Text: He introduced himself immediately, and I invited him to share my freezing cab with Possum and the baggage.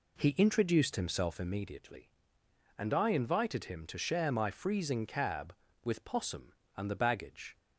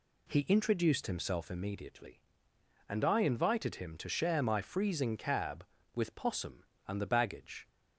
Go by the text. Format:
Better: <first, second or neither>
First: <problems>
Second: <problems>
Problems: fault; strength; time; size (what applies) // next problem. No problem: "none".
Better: second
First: starts louder than the rest; slight; until 1.8 s; 3 dB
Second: none